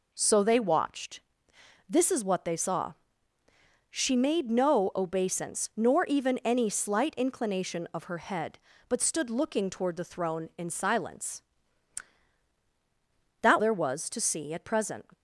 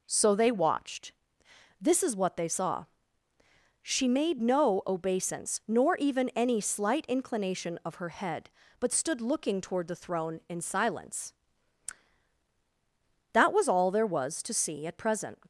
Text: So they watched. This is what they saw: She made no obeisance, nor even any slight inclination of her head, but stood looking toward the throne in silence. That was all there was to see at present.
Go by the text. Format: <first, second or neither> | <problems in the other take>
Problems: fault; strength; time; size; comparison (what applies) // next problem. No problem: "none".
second | skips "was all"; at 13.5 s